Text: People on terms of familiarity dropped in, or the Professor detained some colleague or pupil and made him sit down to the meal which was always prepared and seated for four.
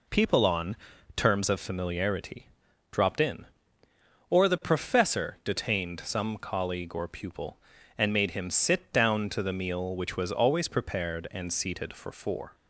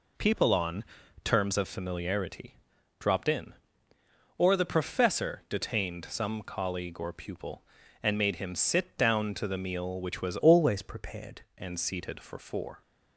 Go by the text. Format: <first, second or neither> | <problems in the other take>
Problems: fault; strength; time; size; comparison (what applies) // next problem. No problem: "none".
first | pauses between "on" and "terms"; at 0.8 s; 0.40 s long; also in the first // pauses between "familiarity" and "dropped"; at 2.5 s; 0.44 s long; also in the first // changes voice from "always" to "prepared"; from 10.3 to 11.4 s; 1.1 s long